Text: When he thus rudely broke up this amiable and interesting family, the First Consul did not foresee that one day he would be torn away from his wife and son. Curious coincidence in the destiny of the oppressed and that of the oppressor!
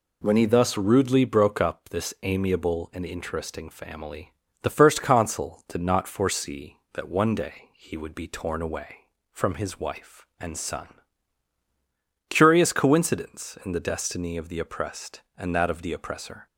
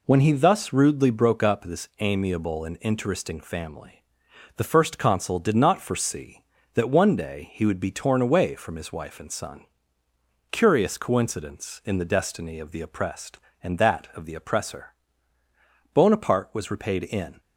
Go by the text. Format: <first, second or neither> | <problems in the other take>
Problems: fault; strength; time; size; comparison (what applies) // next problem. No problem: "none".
first | goes on to say "Bonaparte was repaid in"; from 15.9 s on; 1.4 s long